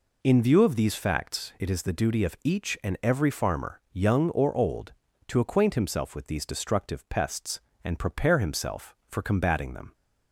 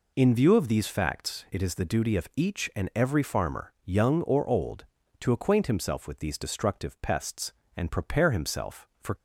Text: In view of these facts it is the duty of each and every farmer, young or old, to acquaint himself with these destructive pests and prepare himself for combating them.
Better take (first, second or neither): first